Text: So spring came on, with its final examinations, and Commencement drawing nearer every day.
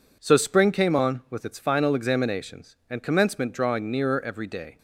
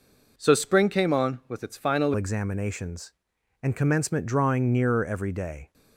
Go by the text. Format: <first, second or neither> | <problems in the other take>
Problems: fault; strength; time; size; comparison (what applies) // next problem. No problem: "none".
first | changes voice at "examinations"; from 2.1 s on; 3.6 s long